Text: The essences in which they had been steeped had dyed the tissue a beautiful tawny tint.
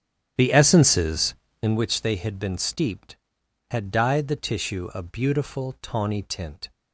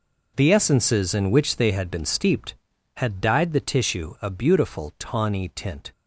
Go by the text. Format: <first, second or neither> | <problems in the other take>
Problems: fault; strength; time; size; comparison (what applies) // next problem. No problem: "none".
second | starts louder than the rest; strong; until 1.8 s; 10 dB